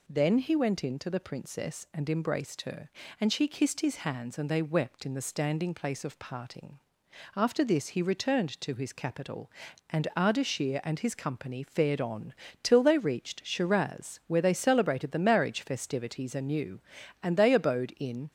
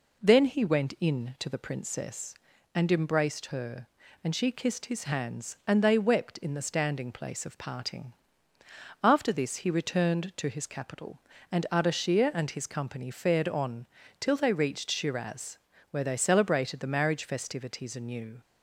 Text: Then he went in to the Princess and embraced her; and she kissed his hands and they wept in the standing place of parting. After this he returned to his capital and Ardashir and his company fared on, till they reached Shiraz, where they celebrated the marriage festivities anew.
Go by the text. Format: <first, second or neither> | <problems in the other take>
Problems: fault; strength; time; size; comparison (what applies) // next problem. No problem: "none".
second | goes on to say "And they abode in"; noticeable; from 17.2 s on; 1.0 s long